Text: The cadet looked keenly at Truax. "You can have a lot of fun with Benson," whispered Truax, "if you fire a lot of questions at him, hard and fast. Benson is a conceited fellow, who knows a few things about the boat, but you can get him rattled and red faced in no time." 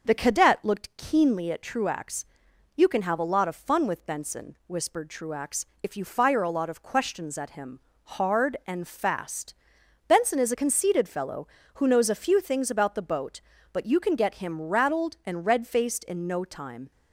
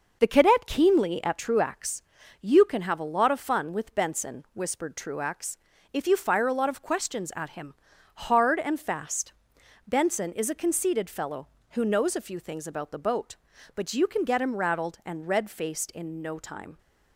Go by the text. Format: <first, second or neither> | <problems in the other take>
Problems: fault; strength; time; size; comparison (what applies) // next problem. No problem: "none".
first | skips "looked"; at 0.6 s